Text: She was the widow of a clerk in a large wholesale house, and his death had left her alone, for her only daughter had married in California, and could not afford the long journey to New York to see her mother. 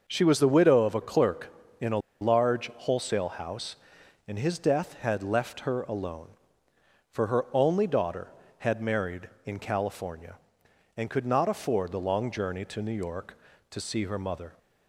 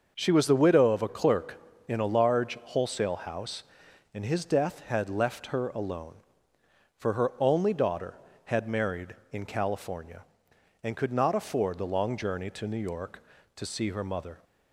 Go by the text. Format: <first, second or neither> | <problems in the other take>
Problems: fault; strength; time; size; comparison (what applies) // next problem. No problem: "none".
second | starts louder than the rest; noticeable; until 1.0 s; 6 dB; also in the second // pauses between "a" and "large"; slight; at 1.9 s; 0.23 s long